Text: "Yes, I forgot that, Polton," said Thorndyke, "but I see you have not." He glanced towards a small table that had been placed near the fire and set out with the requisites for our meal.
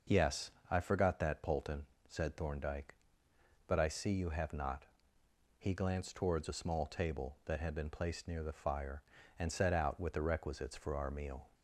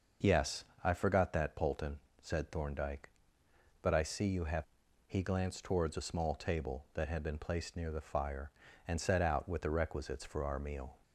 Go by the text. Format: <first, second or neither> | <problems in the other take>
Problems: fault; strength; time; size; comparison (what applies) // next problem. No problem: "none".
first | starts louder than the rest; noticeable; until 1.4 s; 6 dB // skips "not"; at 4.8 s